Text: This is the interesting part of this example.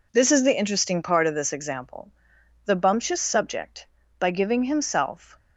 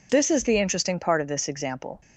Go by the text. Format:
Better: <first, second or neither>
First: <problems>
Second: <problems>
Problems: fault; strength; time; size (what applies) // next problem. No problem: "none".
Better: second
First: goes on to say "The bumptious subject by giving himself"; strong; from 2.6 s on; 2.7 s long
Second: none